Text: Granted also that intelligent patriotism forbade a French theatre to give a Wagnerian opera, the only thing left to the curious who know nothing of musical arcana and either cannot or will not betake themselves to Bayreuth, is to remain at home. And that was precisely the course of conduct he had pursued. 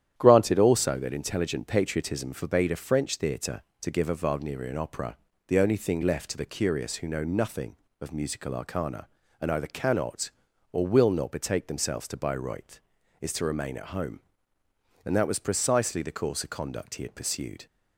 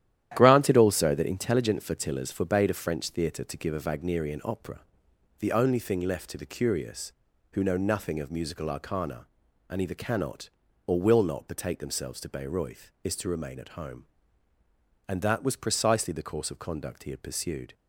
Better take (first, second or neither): first